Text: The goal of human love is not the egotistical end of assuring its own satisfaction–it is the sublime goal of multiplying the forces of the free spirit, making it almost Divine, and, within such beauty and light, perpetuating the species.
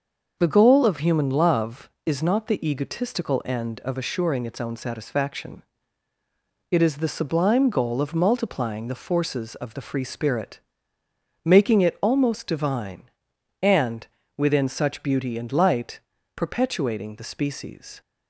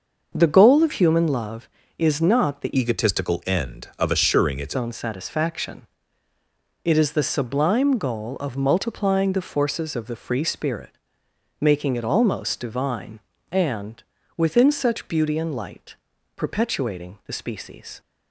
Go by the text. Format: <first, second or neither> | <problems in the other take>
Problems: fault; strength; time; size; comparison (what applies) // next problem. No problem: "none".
first | starts louder than the rest; noticeable; until 1.3 s; 6 dB; also in the first // changes voice from "egotistical" to "its"; from 2.7 to 4.7 s; 2.0 s long